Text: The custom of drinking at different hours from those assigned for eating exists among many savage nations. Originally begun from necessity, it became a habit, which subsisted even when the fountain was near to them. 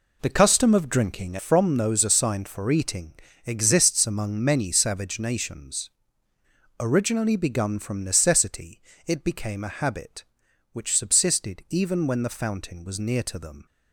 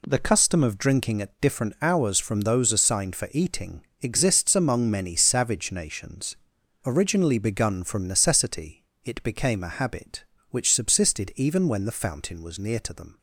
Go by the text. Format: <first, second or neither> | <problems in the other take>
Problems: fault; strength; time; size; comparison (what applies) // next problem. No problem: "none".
second | skips "at different hours"; at 1.3 s // pauses between "eating" and "exists"; slight; at 3.1 s; 0.32 s long; slight in the second